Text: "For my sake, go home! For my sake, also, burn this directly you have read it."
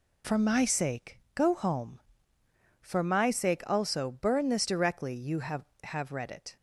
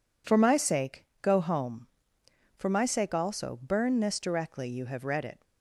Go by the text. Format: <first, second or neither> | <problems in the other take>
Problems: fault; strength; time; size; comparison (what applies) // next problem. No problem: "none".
second | says "have" twice; at 5.8 s